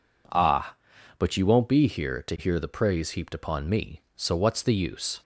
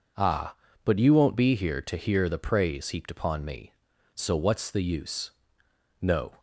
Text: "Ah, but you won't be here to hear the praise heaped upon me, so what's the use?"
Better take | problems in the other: first | goes on to say "No"; slight; from 6.0 s on; 0.38 s long

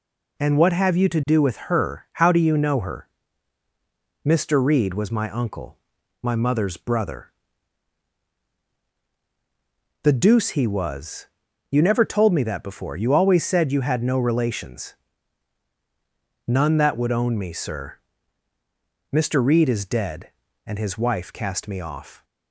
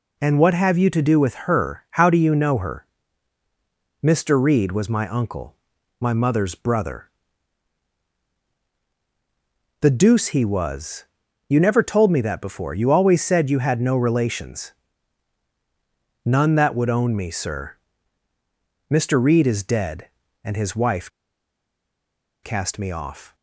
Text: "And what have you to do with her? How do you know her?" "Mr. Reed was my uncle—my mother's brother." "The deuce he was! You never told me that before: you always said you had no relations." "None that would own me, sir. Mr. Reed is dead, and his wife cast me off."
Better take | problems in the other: first | pauses between "wife" and "cast"; strong; at 21.0 s; 1.3 s long

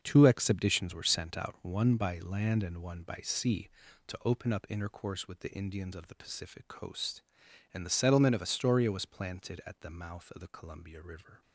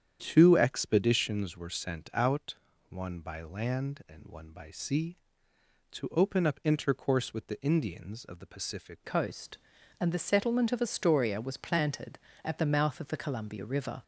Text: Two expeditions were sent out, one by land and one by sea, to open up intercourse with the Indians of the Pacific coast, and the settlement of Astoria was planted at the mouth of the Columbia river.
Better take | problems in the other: first | starts louder than the rest; strong; until 1.2 s; 9 dB; also in the first // changes voice at "coast"; from 9.0 s on; 5.0 s long

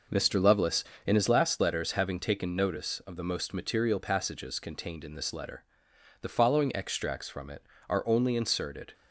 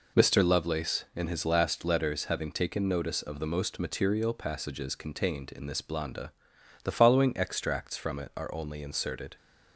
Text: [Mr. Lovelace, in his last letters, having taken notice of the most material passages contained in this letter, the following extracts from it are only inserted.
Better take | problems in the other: first | says "blanda" for "letter"; at 5.8 s

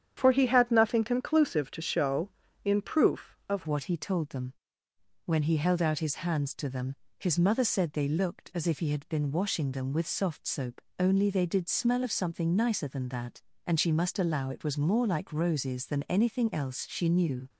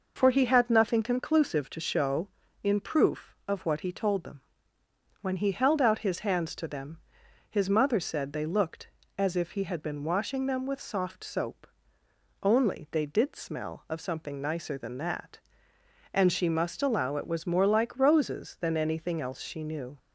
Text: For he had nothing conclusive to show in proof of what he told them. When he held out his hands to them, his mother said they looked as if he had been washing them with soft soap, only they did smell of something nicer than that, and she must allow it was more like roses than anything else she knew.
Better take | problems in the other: second | starts louder than the rest; strong; until 1.1 s; 9 dB // changes voice at "what"; from 3.6 s on; 13.8 s long

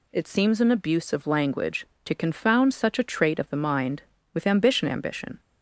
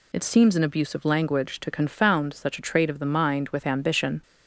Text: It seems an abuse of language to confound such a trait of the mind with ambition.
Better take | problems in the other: second | says "ambition" twice; at 4.8 s

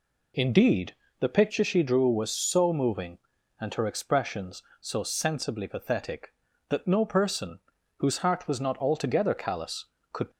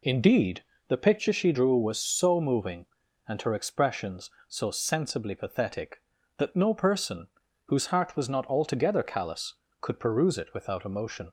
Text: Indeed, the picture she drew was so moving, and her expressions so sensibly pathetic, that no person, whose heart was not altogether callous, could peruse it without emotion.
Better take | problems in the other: second | stops before "peruse it without emotion"; at 10.3 s

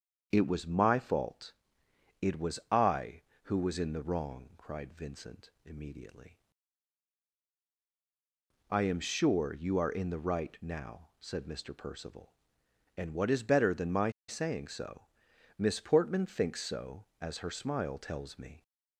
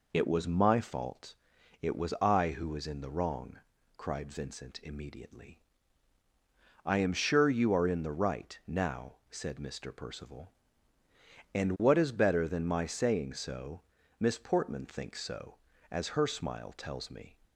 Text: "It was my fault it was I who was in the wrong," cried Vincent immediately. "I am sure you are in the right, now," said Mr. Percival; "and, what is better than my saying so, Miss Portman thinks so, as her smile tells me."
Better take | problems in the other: second | starts louder than the rest; strong; until 1.3 s; 7.5 dB // pauses between "fault" and "it"; noticeable; at 1.5 s; 0.68 s long; noticeable in the second // pauses between "my" and "saying"; slight; at 14.1 s; 0.18 s long

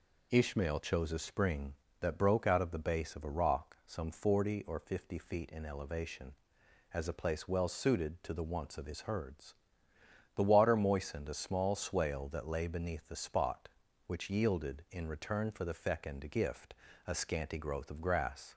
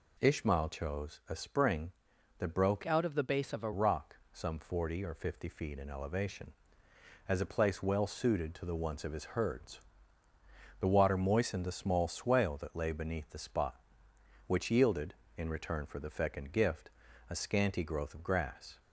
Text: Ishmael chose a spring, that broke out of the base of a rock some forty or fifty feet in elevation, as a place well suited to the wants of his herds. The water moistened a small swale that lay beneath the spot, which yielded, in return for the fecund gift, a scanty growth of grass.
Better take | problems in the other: first | changes voice from "out" to "a"; from 2.8 to 3.7 s; 0.9 s long // pauses between "rock" and "some"; slight; at 4.1 s; 0.16 s long

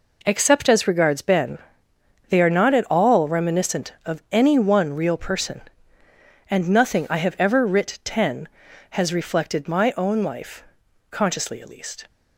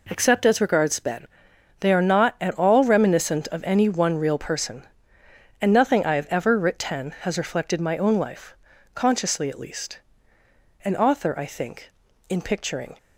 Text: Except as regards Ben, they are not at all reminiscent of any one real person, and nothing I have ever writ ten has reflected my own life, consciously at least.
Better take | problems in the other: first | goes on to say "An author I think in picturing"; strong; from 10.8 s on; 2.1 s long

